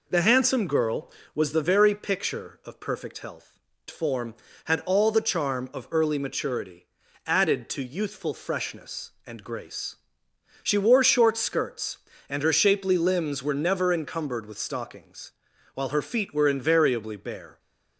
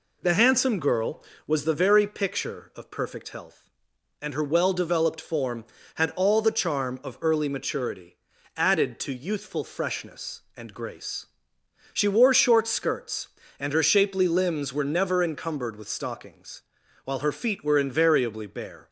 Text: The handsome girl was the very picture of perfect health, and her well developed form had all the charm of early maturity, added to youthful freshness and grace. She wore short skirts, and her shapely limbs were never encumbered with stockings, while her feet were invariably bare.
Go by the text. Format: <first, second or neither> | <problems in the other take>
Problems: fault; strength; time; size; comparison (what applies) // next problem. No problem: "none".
second | skips "and her well developed"; at 3.7 s